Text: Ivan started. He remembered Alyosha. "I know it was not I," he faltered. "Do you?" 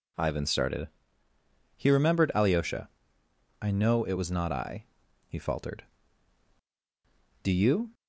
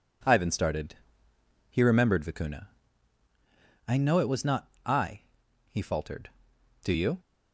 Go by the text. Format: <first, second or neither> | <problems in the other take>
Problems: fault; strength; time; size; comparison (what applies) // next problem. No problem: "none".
first | says "Vicuna" for "Alyosha"; at 2.2 s // pauses between "not" and "I"; slight; at 4.6 s; 0.18 s long